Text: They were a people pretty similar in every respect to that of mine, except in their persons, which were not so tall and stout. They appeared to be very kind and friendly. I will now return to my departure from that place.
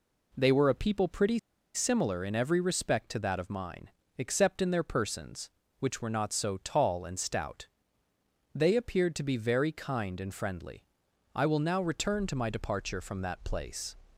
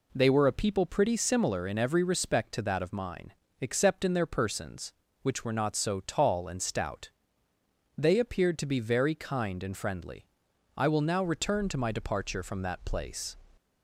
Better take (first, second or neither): second